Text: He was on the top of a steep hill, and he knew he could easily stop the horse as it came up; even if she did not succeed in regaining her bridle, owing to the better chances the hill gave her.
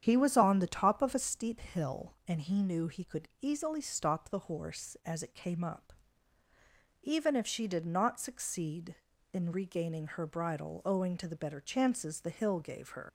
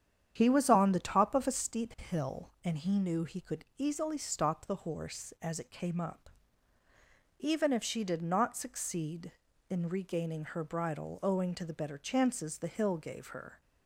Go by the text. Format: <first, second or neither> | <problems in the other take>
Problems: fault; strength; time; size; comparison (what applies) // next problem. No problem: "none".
second | starts louder than the rest; strong; until 1.0 s; 9 dB; strong in the second // leaves "her" unfinished; at 13.0 s; 130 ms